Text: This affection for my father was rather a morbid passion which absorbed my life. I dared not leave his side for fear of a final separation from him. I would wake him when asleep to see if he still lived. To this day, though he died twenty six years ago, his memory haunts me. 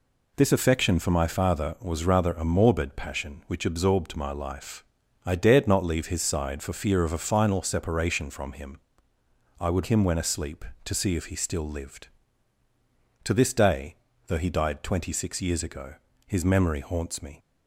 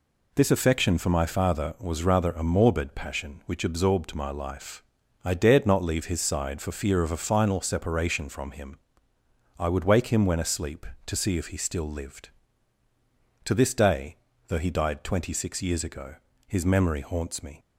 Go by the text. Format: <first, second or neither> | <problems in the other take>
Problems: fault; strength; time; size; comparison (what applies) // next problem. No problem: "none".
second | skips "wake"; at 9.8 s